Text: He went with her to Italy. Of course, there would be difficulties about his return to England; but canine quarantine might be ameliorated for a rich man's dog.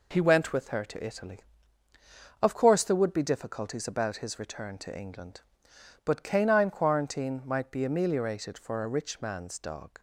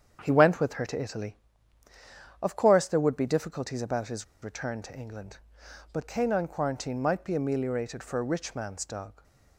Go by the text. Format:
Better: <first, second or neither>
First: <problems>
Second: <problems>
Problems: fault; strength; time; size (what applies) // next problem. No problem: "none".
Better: first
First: none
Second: starts louder than the rest; strong; until 1.2 s; 8 dB // pauses between "his" and "return"; slight; at 4.2 s; 0.18 s long